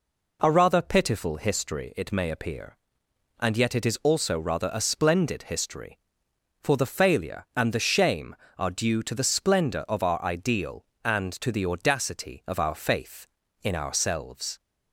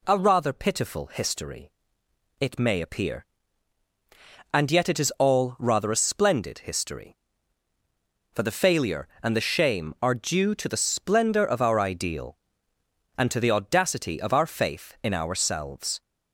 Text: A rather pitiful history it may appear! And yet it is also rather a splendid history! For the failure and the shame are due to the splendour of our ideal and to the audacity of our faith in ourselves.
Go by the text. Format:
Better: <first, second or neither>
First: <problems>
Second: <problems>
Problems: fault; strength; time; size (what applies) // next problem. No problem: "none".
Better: first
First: none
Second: pauses between "history" and "it"; noticeable; at 1.6 s; 0.72 s long // says "all" for "also"; at 5.1 s